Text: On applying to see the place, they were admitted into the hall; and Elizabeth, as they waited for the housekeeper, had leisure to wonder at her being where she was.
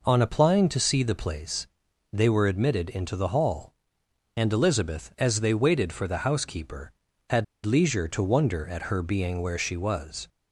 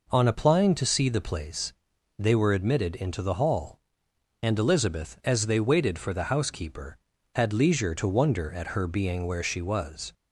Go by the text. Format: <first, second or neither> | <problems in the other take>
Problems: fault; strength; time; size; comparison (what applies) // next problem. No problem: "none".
second | pauses between "had" and "leisure"; slight; at 7.4 s; 0.19 s long